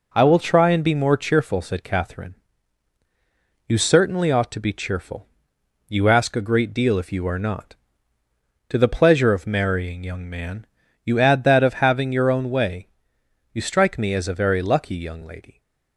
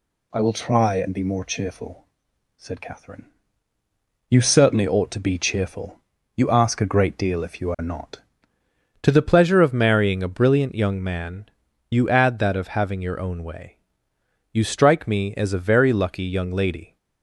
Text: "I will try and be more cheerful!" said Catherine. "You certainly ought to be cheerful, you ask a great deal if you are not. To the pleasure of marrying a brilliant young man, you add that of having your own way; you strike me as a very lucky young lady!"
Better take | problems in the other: second | skips "a brilliant"; at 10.0 s

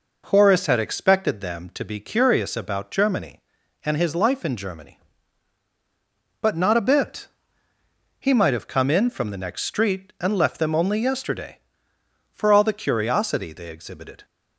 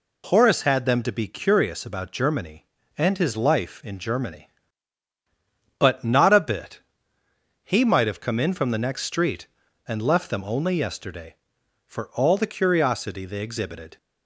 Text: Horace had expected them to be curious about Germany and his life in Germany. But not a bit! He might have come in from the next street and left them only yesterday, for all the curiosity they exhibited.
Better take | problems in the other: first | skips "expected"; at 0.8 s

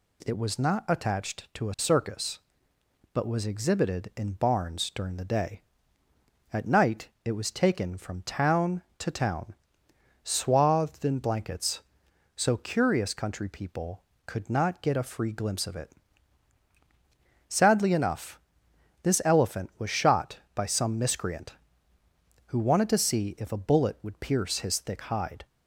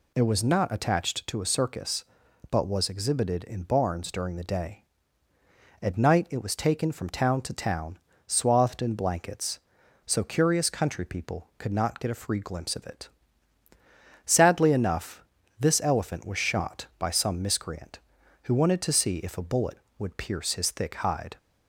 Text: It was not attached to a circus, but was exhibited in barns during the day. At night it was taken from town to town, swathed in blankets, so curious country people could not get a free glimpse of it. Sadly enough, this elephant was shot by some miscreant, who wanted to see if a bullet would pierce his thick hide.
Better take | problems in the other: neither | none

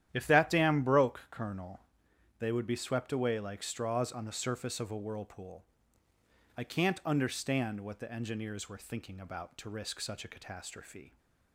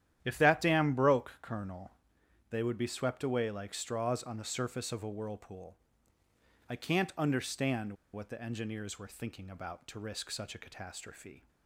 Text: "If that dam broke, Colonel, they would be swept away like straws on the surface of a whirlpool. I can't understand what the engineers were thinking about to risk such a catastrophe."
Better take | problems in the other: first | starts louder than the rest; strong; until 1.2 s; 11 dB; strong in the first // pauses between "understand" and "what"; slight; at 7.9 s; 0.19 s long

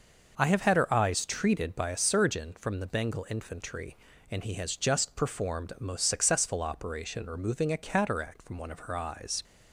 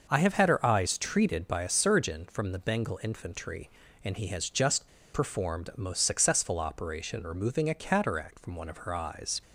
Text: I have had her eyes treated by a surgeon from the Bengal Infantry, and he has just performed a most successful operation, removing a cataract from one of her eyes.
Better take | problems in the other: first | starts louder than the rest; noticeable; until 1.1 s; 6 dB; noticeable in the first // pauses between "just" and "performed"; slight; at 4.8 s; 0.25 s long

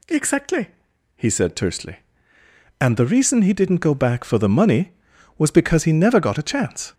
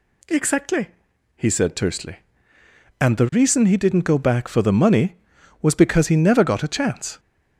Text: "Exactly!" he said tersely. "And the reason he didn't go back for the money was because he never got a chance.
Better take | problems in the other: neither | none

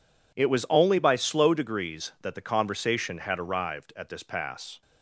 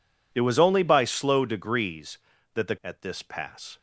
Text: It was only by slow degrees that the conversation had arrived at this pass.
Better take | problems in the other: first | skips "conversation had arrived"; at 2.7 s

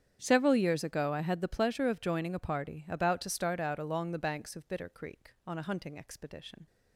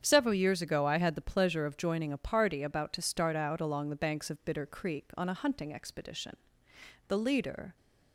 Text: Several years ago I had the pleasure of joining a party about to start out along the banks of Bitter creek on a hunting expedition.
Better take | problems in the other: first | starts louder than the rest; strong; until 1.0 s; 8 dB; strong in the first // goes on to say "The leader"; noticeable; from 7.0 s on; 0.70 s long

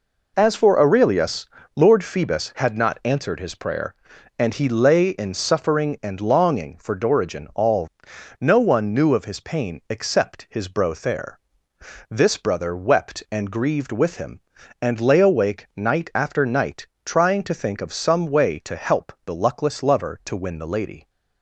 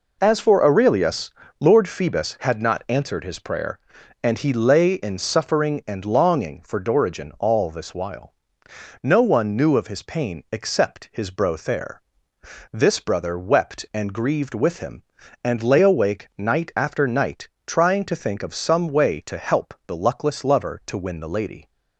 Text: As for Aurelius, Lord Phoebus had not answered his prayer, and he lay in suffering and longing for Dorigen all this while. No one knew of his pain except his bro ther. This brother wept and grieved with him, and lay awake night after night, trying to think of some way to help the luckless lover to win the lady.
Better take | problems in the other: second | skips "this while"; at 8.1 s

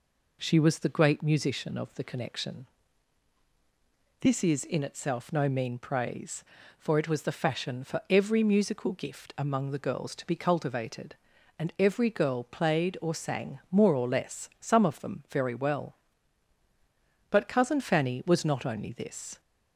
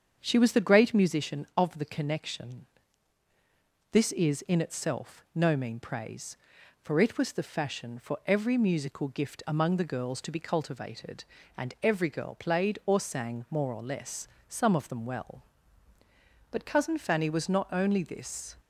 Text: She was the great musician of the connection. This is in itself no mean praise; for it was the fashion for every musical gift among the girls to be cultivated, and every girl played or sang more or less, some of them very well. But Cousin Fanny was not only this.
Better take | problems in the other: first | starts louder than the rest; strong; until 1.2 s; 7.5 dB // skips "very"; at 15.0 s

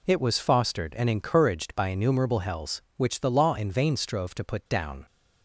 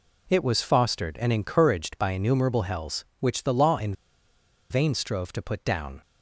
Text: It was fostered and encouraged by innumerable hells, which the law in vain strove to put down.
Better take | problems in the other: first | pauses between "in" and "vain"; noticeable; at 3.9 s; 0.77 s long

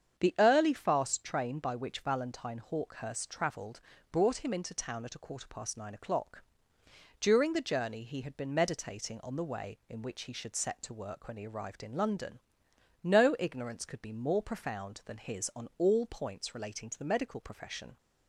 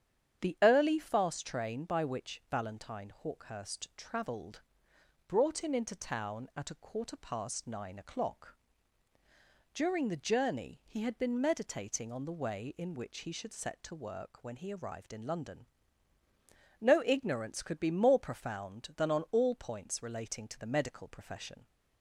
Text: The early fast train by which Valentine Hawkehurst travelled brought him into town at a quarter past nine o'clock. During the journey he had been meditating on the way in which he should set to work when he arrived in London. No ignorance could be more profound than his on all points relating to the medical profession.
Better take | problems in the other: first | starts louder than the rest; strong; until 1.4 s; 8.5 dB; strong in the first // pauses between "travelled" and "brought"; noticeable; at 4.6 s; 0.66 s long; slight in the first // skips "his"; at 19.0 s

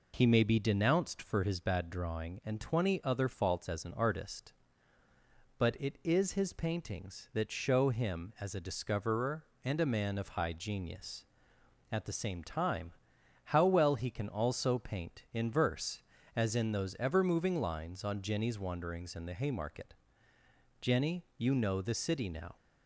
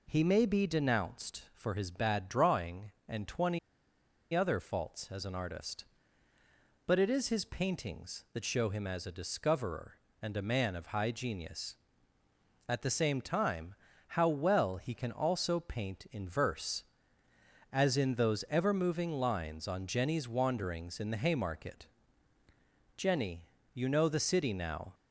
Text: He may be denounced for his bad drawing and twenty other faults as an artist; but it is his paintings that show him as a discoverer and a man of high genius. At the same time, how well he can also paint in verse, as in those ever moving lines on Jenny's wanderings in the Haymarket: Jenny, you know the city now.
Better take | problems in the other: first | pauses between "twenty" and "other"; noticeable; at 3.5 s; 0.74 s long

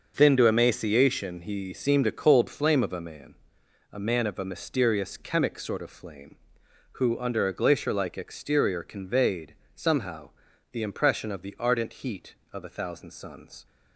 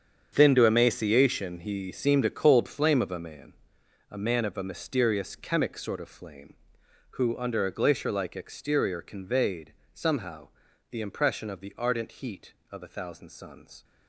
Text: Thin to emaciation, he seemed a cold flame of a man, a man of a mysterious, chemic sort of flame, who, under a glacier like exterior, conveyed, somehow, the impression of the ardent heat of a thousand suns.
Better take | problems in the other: first | gets quieter; strong; throughout; 13 dB // starts louder than the rest; strong; until 1.3 s; 7.5 dB; also in the first

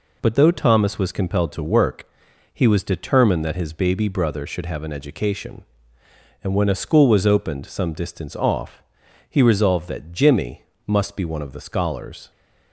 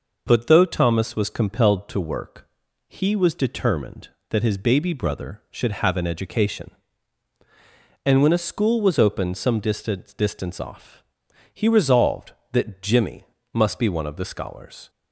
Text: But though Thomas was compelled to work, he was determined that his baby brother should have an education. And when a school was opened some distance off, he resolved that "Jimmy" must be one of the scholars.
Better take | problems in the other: first | says "distance" twice; at 10.1 s // pauses between "Jimmy" and "must"; slight; at 13.2 s; 0.30 s long; slight in the first

